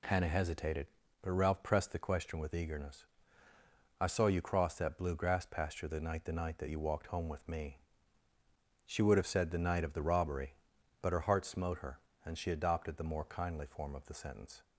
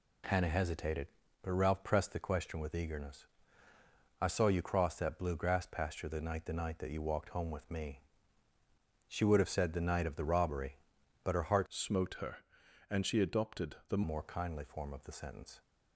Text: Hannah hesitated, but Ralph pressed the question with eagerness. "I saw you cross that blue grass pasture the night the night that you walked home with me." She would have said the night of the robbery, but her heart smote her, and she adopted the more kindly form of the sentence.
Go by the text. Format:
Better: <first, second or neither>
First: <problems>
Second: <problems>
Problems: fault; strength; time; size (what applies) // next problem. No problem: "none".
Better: first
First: none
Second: changes voice from "smote" to "the"; from 11.6 to 14.0 s; 2.4 s long